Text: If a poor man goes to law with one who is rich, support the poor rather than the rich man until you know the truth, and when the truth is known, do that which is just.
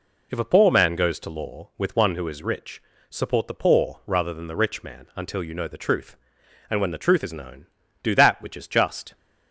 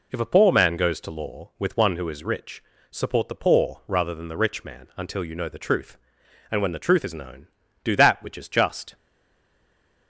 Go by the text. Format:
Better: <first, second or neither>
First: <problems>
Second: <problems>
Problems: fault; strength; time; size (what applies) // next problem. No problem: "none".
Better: first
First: none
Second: stays silent after the last word; from 8.9 s on; 1.1 s long